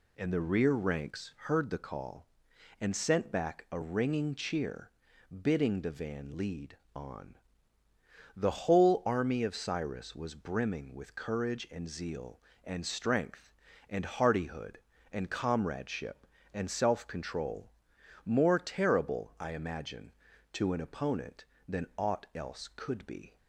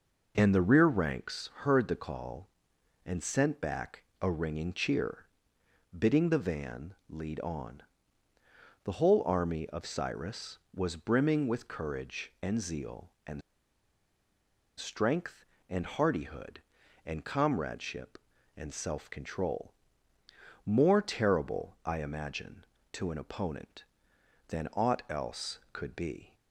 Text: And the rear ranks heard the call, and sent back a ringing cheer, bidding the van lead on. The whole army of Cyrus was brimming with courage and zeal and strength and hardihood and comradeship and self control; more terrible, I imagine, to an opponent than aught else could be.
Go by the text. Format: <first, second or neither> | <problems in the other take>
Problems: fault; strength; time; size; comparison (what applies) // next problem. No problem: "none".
first | pauses between "back" and "a"; slight; at 4.0 s; 0.18 s long // pauses between "van" and "lead"; slight; at 6.9 s; 0.16 s long // pauses between "and" and "strength"; strong; at 13.4 s; 1.3 s long